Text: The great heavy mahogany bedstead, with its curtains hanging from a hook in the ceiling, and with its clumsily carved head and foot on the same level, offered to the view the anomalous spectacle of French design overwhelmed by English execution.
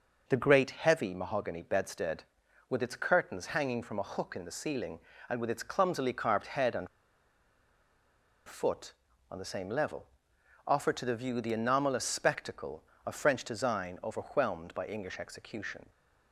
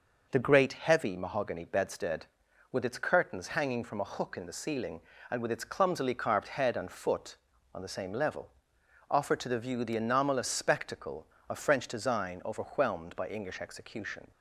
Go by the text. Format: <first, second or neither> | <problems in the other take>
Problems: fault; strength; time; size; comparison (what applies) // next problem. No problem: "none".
second | pauses between "and" and "foot"; strong; at 6.8 s; 1.6 s long